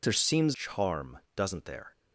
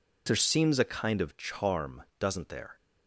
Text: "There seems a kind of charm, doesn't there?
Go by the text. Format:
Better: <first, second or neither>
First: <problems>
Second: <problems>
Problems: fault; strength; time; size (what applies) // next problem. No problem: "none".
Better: second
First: skips "a kind of"; at 0.5 s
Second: none